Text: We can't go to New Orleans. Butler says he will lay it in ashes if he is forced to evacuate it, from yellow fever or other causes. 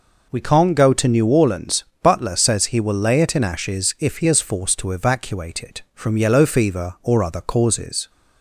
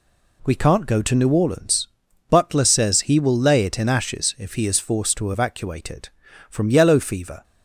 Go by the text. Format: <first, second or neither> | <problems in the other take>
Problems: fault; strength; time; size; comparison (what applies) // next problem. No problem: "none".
first | stops before "or other causes"; at 7.4 s